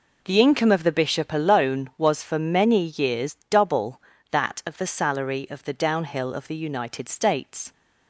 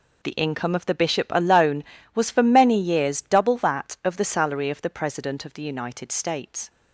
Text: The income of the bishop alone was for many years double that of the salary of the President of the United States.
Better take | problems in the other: second | says "Downhill" for "President"; at 5.7 s

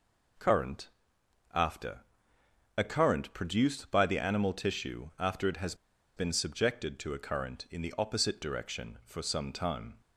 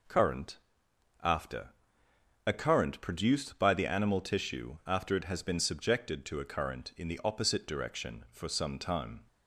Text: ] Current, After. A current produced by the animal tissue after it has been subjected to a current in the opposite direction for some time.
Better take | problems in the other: second | pauses between "has" and "been"; at 5.7 s; 0.42 s long

